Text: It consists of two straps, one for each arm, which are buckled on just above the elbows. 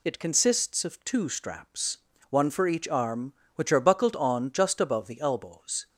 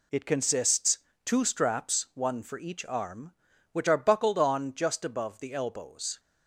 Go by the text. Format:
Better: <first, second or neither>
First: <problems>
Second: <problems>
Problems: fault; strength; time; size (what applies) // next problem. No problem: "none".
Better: first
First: none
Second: skips "of"; at 1.1 s